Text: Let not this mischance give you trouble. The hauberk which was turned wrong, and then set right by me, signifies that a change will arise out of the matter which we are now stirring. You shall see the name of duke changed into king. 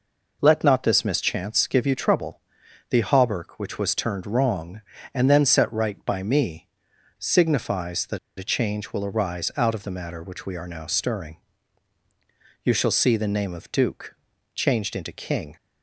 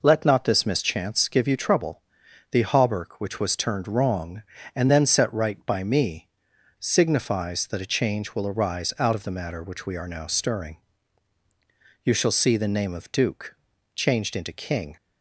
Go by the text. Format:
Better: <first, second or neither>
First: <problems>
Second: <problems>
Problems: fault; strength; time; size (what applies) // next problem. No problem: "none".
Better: second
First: pauses between "that" and "a"; slight; at 8.1 s; 0.21 s long // pauses between "duke" and "changed"; at 14.1 s; 0.40 s long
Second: pauses between "duke" and "changed"; at 13.5 s; 0.40 s long